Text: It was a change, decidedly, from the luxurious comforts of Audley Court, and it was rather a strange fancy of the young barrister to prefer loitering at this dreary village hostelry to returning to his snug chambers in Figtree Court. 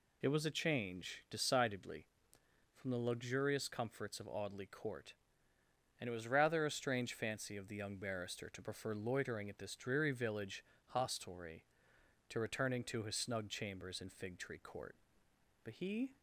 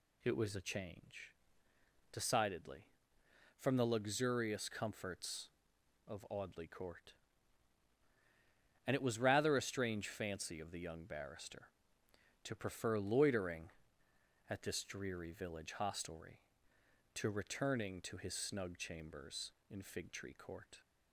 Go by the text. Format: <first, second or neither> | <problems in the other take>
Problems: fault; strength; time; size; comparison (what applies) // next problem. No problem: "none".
second | pauses between "village" and "hostelry"; slight; at 10.6 s; 0.26 s long // goes on to say "But he"; from 15.6 s on; 0.54 s long